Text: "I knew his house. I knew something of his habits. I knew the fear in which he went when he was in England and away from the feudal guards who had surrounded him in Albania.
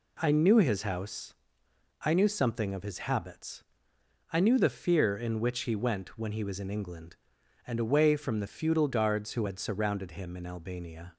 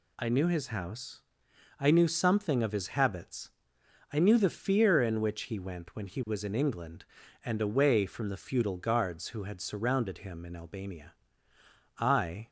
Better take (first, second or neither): first